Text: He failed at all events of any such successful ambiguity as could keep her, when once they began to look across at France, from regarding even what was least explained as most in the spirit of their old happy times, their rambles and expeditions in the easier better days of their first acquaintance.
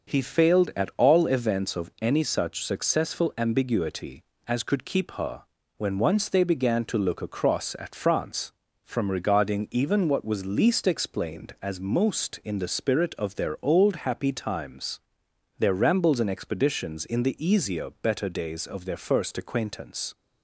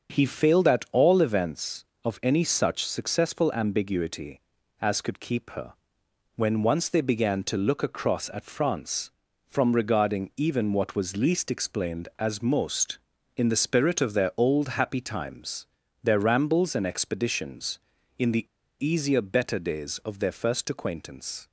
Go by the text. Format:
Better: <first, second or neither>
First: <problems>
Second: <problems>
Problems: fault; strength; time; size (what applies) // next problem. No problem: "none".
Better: first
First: starts louder than the rest; until 1.2 s; 6 dB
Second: starts louder than the rest; until 1.1 s; 6.5 dB // pauses between "the" and "easier"; slight; at 18.4 s; 0.35 s long